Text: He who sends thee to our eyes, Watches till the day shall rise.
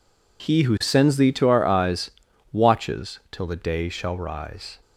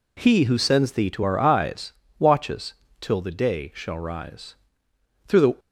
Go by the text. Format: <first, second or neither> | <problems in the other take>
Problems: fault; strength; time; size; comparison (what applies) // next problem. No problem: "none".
first | pauses between "Watches" and "till"; slight; at 2.7 s; 0.30 s long // goes on to say "Through the"; slight; from 5.2 s on; 0.28 s long